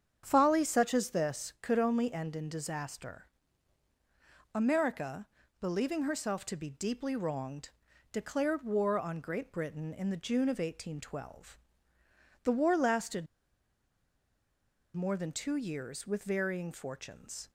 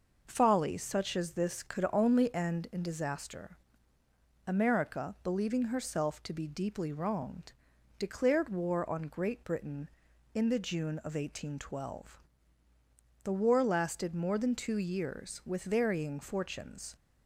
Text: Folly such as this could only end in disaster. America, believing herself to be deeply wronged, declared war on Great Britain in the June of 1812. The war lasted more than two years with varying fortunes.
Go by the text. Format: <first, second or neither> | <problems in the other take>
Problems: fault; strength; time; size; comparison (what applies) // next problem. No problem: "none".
second | starts louder than the rest; strong; until 1.2 s; 8 dB // pauses between "lasted" and "more"; strong; at 13.2 s; 1.6 s long